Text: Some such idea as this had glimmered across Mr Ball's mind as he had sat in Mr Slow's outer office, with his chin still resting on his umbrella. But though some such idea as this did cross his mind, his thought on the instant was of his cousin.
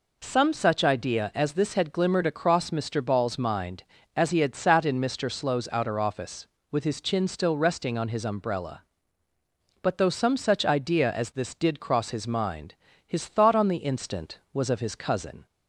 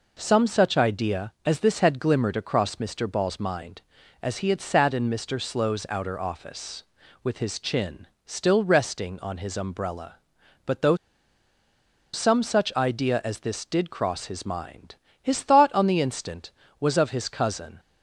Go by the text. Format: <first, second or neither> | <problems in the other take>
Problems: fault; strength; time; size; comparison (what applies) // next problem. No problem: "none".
first | pauses between "chin" and "still"; slight; at 8.0 s; 0.18 s long // pauses between "though" and "some"; at 10.9 s; 1.1 s long